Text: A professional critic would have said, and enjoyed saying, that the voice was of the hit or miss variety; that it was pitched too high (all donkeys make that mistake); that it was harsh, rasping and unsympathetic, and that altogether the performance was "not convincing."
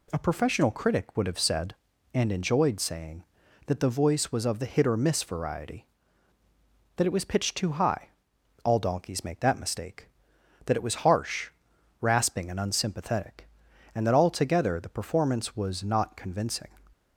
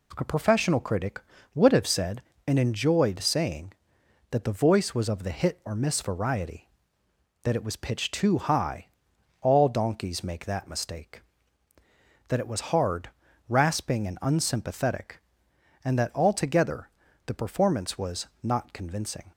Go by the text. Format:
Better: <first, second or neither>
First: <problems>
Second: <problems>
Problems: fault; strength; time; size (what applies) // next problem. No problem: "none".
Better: first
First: none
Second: says "hard" for "harsh"; at 12.7 s // pauses between "altogether" and "the"; slight; at 16.8 s; 0.36 s long // pauses between "was" and "not"; slight; at 18.2 s; 0.16 s long